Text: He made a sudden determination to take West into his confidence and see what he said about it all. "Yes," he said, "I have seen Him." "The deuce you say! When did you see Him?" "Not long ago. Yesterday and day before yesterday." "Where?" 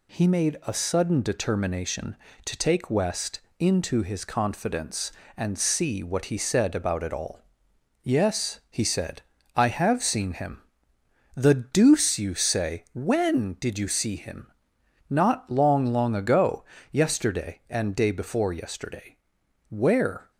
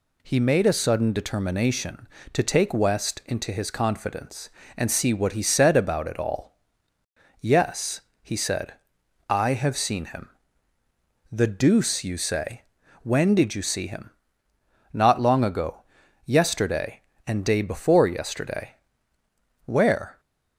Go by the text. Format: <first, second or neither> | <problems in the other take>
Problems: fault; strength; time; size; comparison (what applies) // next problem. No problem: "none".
second | pauses between "West" and "into"; slight; at 3.3 s; 0.22 s long // says "long" twice; at 15.8 s